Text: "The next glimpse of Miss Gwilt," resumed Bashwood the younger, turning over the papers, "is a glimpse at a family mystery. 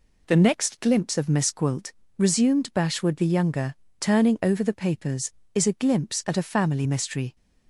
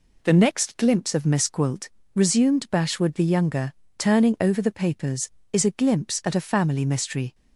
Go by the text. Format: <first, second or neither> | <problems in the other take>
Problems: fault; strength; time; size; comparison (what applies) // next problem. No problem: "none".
neither | none